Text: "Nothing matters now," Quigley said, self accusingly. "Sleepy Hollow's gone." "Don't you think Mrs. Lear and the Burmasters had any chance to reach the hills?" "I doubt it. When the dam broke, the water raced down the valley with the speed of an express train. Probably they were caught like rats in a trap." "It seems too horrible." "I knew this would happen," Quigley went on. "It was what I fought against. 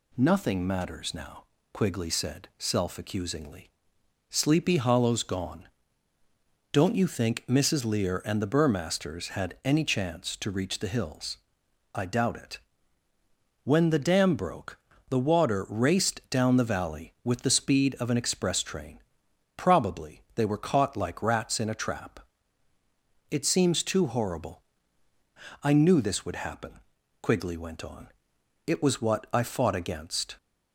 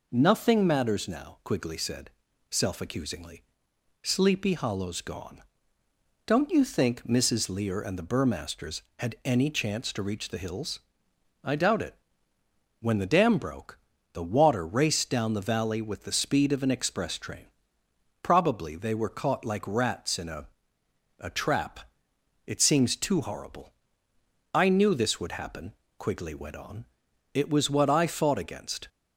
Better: first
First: none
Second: says "a" twice; at 21.1 s

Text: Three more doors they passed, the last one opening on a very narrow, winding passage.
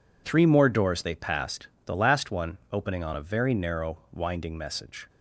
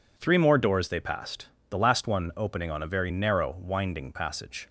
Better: second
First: says "message" for "passage"; at 4.5 s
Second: none

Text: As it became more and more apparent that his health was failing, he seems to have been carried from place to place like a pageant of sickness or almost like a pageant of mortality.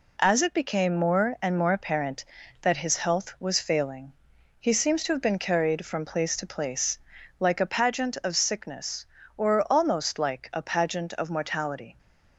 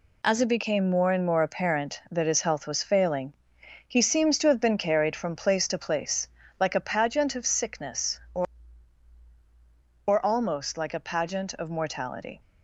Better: first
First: pauses between "place" and "like"; at 6.9 s; 0.40 s long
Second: pauses between "place" and "like"; slight; at 6.2 s; 0.32 s long // says "or" twice; at 10.0 s

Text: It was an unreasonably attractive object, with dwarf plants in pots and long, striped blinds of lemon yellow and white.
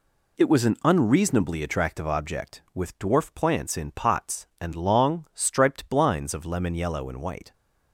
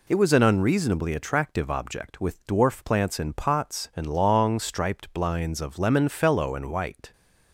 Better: first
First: none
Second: says "fellow" for "yellow"; at 6.0 s

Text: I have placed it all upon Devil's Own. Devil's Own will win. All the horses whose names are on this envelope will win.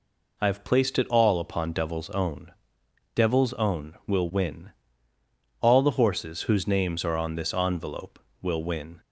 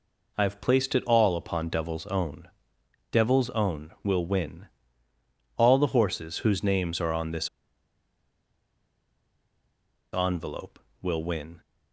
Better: first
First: none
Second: pauses between "this" and "envelope"; strong; at 7.4 s; 2.6 s long

